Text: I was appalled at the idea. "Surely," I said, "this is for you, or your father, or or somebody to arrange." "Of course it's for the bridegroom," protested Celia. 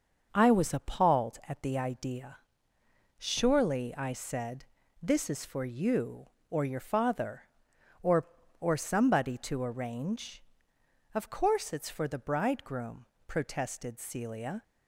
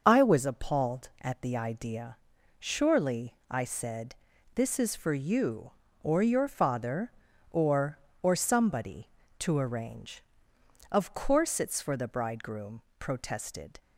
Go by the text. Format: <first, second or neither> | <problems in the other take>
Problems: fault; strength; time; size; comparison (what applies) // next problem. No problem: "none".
first | starts louder than the rest; noticeable; until 1.0 s; 6 dB; also in the first // stops before "Celia"; at 13.7 s